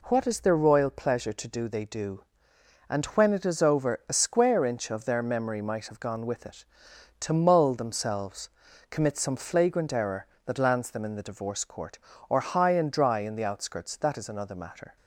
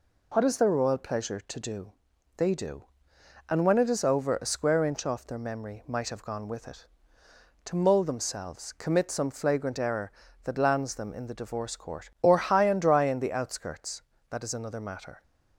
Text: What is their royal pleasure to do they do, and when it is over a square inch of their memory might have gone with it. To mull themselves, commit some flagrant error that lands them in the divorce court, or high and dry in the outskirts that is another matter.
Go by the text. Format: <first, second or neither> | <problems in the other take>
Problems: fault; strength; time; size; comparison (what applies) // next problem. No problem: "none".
first | pauses between "do" and "they"; at 1.9 s; 0.44 s long // says "off" for "of"; at 5.0 s